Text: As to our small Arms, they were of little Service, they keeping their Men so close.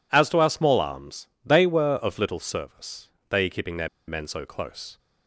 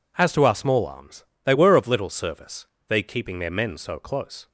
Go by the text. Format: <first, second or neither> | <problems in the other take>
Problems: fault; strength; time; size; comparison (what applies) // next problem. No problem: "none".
second | pauses between "their" and "Men"; slight; at 3.8 s; 0.19 s long